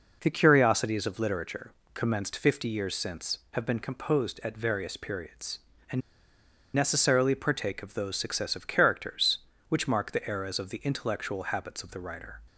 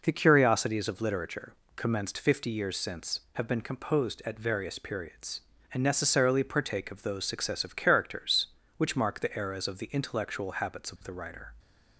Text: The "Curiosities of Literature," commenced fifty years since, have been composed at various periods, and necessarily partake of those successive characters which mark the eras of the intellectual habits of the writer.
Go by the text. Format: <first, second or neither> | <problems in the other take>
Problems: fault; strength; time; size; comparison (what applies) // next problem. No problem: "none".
second | pauses between "and" and "necessarily"; noticeable; at 6.0 s; 0.74 s long